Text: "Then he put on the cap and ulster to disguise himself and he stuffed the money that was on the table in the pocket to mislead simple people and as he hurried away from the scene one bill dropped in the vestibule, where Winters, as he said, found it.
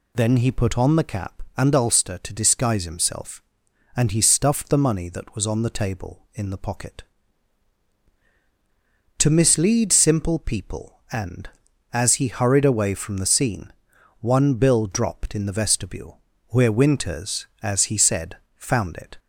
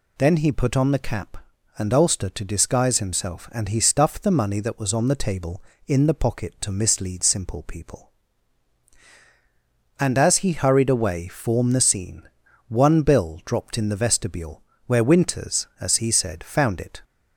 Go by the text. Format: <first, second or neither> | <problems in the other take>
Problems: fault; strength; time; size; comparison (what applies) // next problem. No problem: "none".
first | says "form" for "from"; at 11.2 s // pauses between "scene" and "one"; at 12.2 s; 0.40 s long; noticeable in the first